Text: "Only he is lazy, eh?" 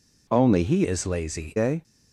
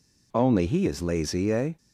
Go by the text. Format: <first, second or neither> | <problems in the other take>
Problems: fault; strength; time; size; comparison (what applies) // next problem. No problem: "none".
second | changes voice from "is" to "lazy"; from 0.8 to 1.5 s; 0.7 s long